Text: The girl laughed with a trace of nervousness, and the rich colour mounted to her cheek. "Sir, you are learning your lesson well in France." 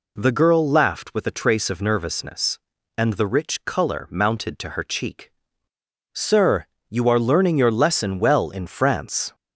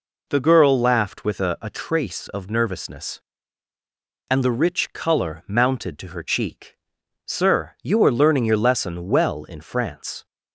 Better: first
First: none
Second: says "a" twice; at 1.6 s

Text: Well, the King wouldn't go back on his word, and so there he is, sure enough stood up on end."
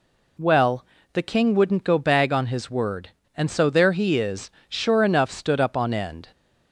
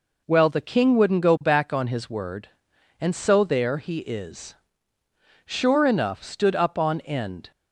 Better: second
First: says "bag" for "back"; at 1.9 s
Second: none

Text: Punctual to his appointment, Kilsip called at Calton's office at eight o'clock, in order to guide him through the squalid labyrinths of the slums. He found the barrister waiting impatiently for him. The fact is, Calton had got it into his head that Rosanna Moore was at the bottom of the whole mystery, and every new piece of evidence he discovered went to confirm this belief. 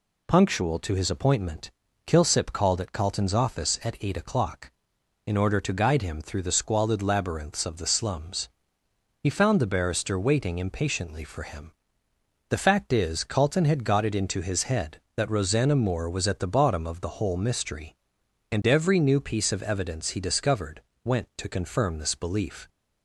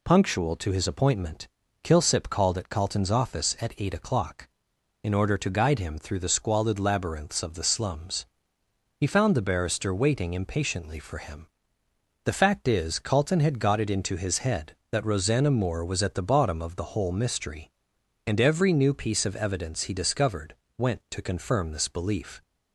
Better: neither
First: pauses between "discovered" and "went"; slight; at 20.8 s; 0.22 s long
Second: pauses between "discovered" and "went"; slight; at 20.5 s; 0.22 s long

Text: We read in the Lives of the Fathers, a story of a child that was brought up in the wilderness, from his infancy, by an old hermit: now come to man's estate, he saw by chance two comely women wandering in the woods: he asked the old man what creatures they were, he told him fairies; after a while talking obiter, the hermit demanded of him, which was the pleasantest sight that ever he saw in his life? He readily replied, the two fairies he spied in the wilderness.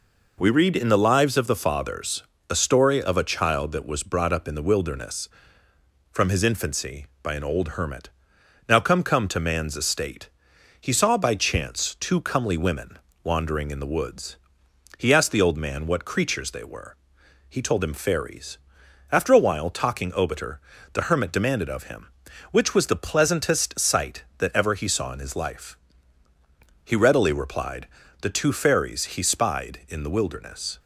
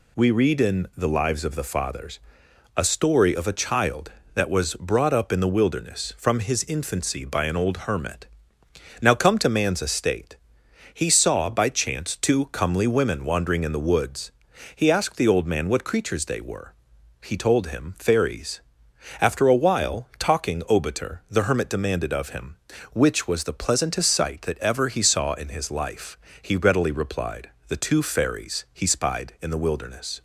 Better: second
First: says "come" twice; at 9.0 s // pauses between "women" and "wandering"; slight; at 12.9 s; 0.26 s long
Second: none

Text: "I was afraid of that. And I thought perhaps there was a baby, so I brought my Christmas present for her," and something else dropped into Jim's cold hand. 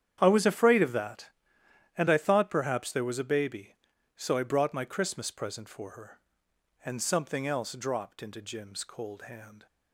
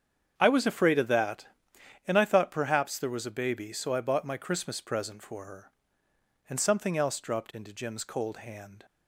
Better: first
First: starts louder than the rest; strong; until 1.2 s; 9 dB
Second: starts louder than the rest; strong; until 1.3 s; 8 dB // says "bought" for "brought"; at 4.0 s

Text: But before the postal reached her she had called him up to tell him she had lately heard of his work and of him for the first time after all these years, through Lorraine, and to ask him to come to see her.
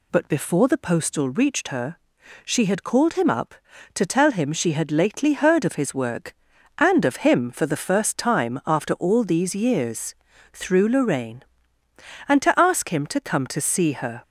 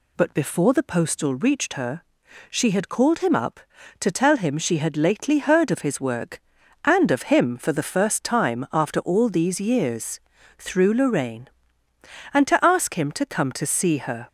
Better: neither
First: pauses between "her" and "she"; noticeable; at 1.9 s; 0.48 s long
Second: pauses between "her" and "she"; noticeable; at 2.0 s; 0.48 s long

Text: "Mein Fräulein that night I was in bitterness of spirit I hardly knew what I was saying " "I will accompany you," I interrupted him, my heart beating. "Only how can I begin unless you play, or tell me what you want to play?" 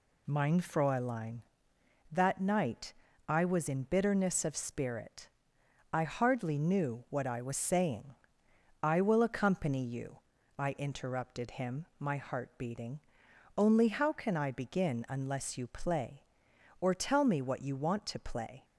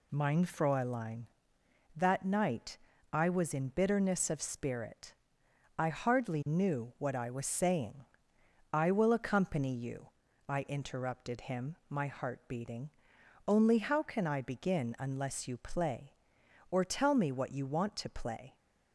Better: neither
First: pauses between "night" and "I"; slight; at 2.9 s; 0.34 s long // pauses between "spirit" and "I"; noticeable; at 5.3 s; 0.64 s long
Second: pauses between "night" and "I"; slight; at 2.7 s; 0.34 s long // pauses between "spirit" and "I"; noticeable; at 5.1 s; 0.64 s long

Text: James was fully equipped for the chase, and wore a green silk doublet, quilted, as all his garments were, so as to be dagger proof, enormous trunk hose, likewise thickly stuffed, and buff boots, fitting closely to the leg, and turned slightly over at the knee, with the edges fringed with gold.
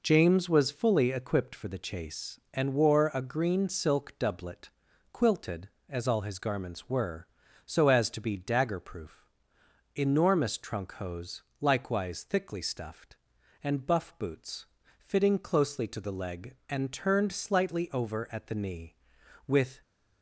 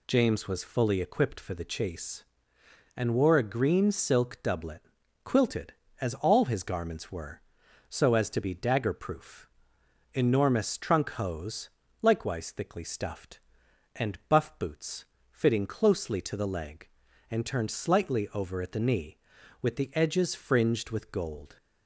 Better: second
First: stops before "the edges fringed with gold"; at 19.8 s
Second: none

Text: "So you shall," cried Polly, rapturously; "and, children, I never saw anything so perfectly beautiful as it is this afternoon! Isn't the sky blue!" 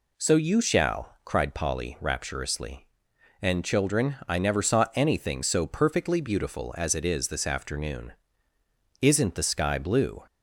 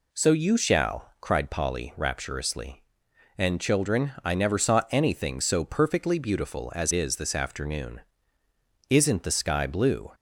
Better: first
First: none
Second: skips "it"; at 6.9 s

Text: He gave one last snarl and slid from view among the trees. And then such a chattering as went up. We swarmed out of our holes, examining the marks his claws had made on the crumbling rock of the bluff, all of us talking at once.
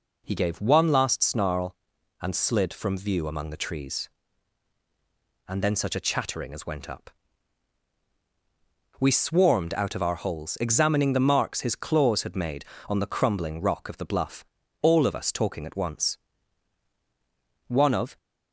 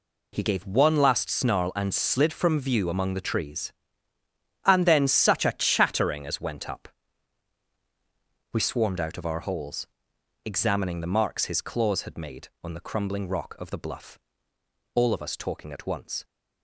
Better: second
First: goes on to say "One of"; from 17.6 s on; 0.50 s long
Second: none

